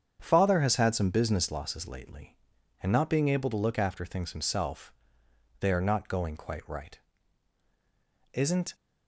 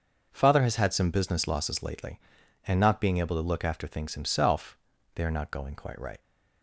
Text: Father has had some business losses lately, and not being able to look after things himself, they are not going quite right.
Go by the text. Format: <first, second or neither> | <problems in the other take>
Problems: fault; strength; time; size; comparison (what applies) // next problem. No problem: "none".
second | starts louder than the rest; strong; until 1.2 s; 8 dB; also in the second // goes on to say "Isn't"; slight; from 8.3 s on; 0.40 s long